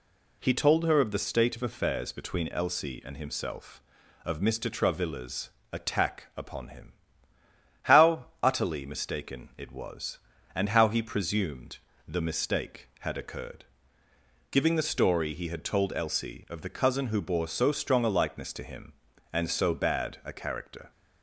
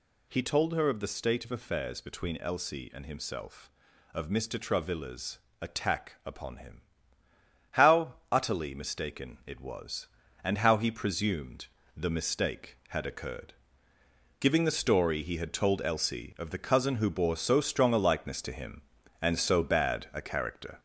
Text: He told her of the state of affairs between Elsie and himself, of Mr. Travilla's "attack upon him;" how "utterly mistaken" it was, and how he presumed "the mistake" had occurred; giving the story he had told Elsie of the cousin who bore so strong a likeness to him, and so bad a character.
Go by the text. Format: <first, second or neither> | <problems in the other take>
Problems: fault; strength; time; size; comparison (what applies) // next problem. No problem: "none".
first | gets louder; noticeable; throughout; 4.5 dB // pauses between "Travilla's" and "attack"; slight; at 5.3 s; 0.20 s long; slight in the first // pauses between "how" and "utterly"; slight; at 8.1 s; 0.18 s long; slight in the first // pauses between "presumed" and "the"; slight; at 11.6 s; 0.32 s long; slight in the first